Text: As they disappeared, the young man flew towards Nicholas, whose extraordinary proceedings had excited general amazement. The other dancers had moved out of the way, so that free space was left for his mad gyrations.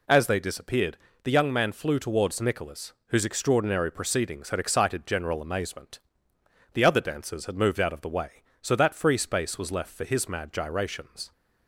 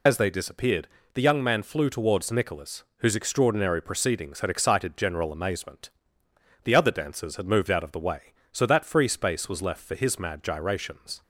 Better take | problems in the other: first | loses the start of "As"; at 0.0 s; 75 ms

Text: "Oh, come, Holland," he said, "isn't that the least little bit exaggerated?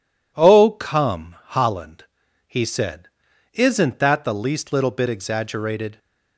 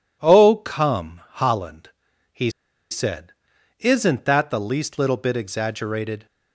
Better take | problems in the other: first | pauses between "he" and "said"; at 2.5 s; 0.40 s long

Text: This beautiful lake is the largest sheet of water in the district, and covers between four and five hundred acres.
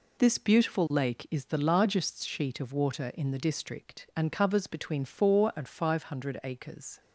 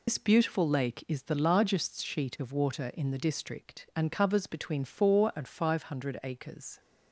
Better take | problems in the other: first | loses the start of "This"; at 0.0 s; 80 ms

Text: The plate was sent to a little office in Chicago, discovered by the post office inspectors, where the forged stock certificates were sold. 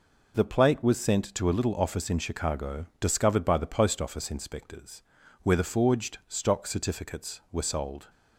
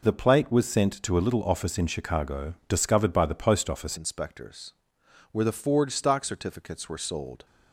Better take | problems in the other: first | changes voice at "inspectors"; from 3.9 s on; 3.5 s long

